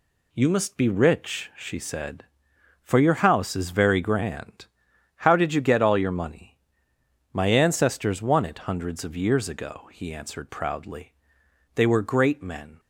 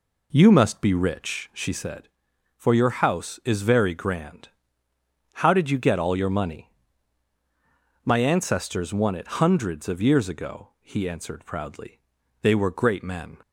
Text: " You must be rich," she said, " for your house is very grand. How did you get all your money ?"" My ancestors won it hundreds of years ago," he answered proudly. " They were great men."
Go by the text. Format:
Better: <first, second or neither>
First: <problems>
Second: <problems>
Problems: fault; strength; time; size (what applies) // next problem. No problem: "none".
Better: first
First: none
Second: starts louder than the rest; slight; until 1.8 s; 3 dB